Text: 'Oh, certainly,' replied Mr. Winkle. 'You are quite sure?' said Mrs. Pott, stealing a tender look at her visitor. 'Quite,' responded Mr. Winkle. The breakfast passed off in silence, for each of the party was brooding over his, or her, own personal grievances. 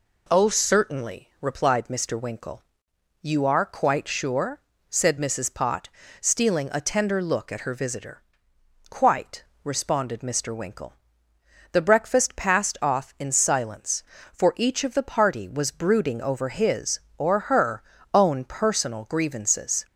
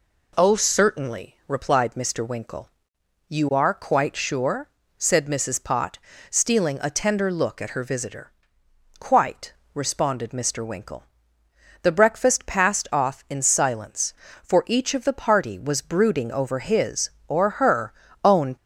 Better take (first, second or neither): first